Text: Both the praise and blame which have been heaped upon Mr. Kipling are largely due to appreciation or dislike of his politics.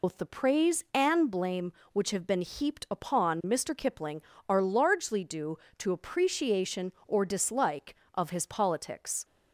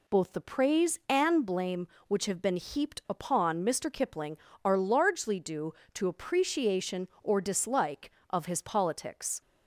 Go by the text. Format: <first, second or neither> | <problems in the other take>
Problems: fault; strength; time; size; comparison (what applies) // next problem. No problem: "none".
second | loses the start of "Both"; at 0.0 s; 100 ms